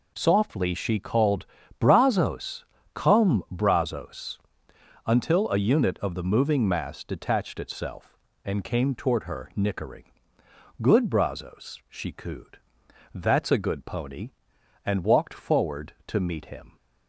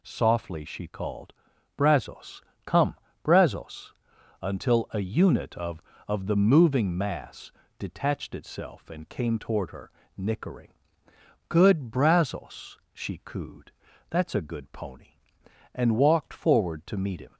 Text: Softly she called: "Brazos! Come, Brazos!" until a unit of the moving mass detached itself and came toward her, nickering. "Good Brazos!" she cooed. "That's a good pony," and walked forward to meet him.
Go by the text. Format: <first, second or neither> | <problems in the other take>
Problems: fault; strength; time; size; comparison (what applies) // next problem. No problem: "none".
first | says "of" twice; at 6.0 s // pauses between "mass" and "detached"; slight; at 7.5 s; 0.26 s long